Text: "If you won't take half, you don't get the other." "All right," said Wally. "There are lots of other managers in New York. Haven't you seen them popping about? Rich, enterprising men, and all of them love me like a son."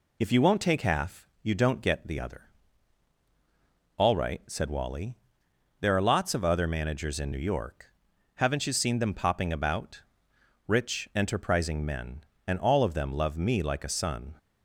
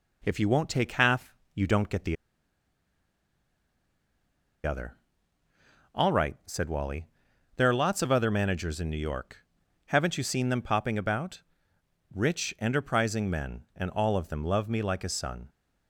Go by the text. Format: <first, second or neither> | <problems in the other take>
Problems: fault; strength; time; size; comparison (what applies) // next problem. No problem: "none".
first | pauses between "the" and "other"; strong; at 2.1 s; 2.4 s long